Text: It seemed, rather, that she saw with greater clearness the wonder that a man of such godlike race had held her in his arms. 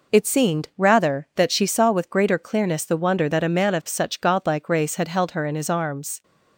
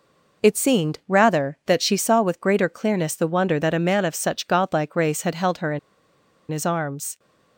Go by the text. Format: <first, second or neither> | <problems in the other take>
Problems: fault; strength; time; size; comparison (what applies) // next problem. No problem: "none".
first | pauses between "in" and "his"; noticeable; at 5.7 s; 0.71 s long